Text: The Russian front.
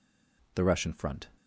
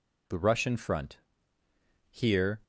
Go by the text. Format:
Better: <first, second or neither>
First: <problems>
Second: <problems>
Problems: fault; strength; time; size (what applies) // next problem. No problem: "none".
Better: first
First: none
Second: goes on to say "Here"; from 2.0 s on; 0.50 s long